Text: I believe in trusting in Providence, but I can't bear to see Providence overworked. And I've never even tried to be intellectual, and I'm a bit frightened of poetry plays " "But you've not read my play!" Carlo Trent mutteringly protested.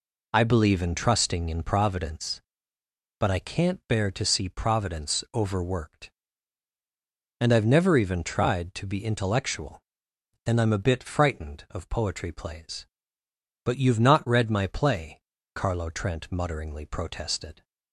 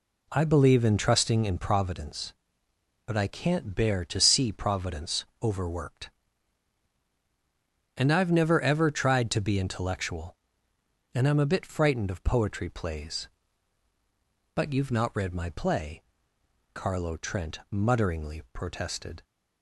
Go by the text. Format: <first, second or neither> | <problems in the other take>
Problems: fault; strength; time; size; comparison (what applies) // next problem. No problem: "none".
first | pauses between "Providence" and "overworked"; slight; at 5.2 s; 0.18 s long // says "ever" for "even"; at 8.5 s